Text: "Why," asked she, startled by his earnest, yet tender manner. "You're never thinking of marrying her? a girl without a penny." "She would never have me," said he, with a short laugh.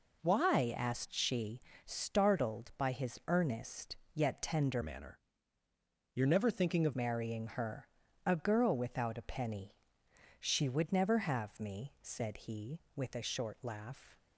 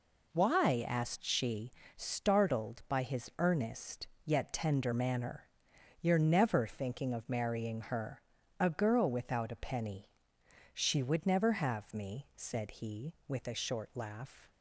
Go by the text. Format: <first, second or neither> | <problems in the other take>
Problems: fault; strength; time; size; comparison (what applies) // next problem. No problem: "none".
second | changes voice from "manner" to "of"; from 4.8 to 6.9 s; 2.1 s long